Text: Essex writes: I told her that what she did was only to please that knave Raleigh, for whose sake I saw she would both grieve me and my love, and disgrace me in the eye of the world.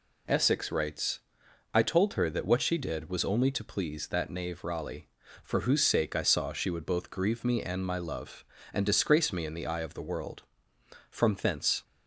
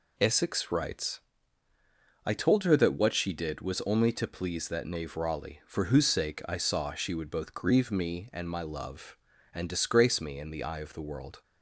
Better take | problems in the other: second | goes on to say "From thence"; noticeable; from 11.0 s on; 0.74 s long

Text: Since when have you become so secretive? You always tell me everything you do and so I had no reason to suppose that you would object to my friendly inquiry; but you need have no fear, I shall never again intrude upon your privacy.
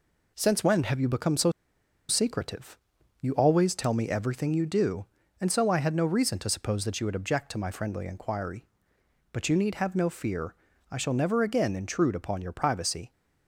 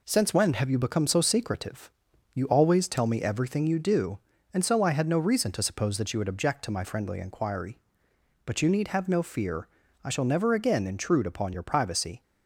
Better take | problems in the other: second | pauses between "so" and "secretive"; noticeable; at 1.5 s; 0.58 s long

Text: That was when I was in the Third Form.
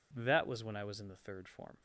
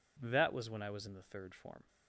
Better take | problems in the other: neither | none

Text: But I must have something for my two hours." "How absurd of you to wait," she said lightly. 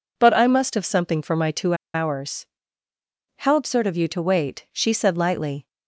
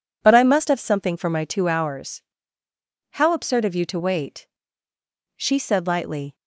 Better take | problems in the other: second | pauses between "two" and "hours"; slight; at 1.7 s; 0.20 s long

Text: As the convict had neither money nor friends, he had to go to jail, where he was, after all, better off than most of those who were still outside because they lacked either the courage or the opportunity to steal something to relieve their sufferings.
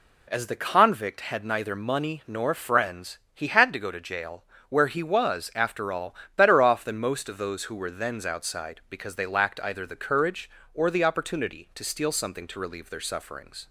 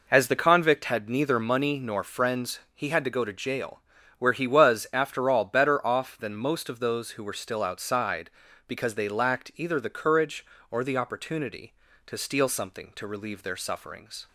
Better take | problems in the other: second | says "thens" for "still"; at 7.9 s

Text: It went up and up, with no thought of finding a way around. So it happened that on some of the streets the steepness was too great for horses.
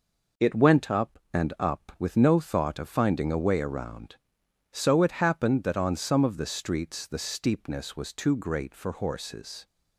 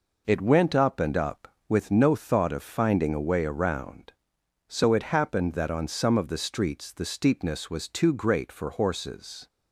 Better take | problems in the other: neither | none

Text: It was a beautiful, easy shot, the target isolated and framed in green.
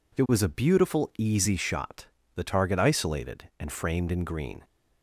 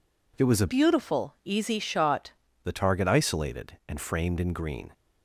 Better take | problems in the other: first | changes voice from "beautiful" to "shot"; from 0.6 to 2.3 s; 1.7 s long

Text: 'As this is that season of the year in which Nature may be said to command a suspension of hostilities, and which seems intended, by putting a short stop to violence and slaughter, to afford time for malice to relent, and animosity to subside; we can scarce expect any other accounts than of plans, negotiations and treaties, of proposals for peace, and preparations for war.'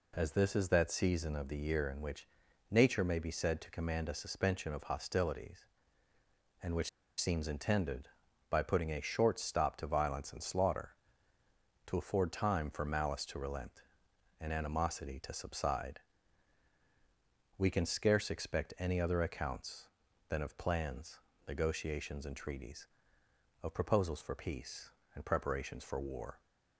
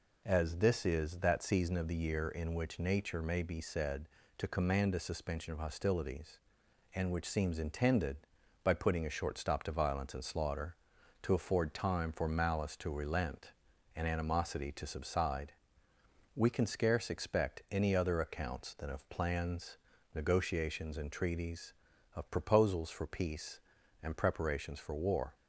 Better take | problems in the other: second | pauses between "which" and "Nature"; at 2.2 s; 0.42 s long // pauses between "which" and "seems"; slight; at 6.8 s; 0.31 s long

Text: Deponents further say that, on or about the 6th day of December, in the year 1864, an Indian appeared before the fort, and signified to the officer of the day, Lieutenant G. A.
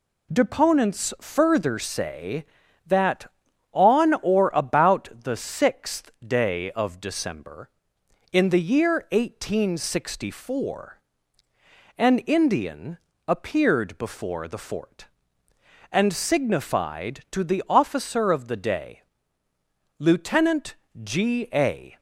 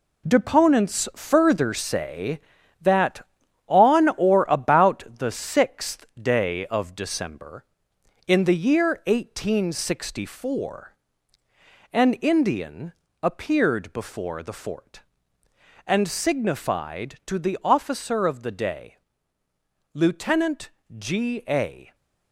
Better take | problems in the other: first | gets quieter; strong; throughout; 8.5 dB // pauses between "Indian" and "appeared"; slight; at 12.9 s; 0.30 s long; slight in the first // pauses between "Lieutenant" and "G"; slight; at 20.7 s; 0.26 s long; slight in the first

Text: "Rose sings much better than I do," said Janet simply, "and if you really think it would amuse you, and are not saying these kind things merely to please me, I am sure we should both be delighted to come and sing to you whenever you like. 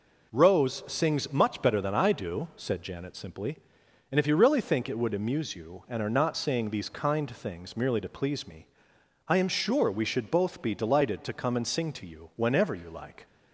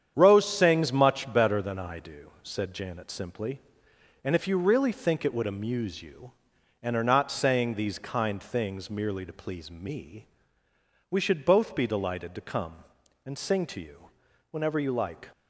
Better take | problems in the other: first | starts louder than the rest; strong; until 1.1 s; 8.5 dB // skips "I am sure"; at 10.6 s // pauses between "you" and "whenever"; at 14.1 s; 0.40 s long

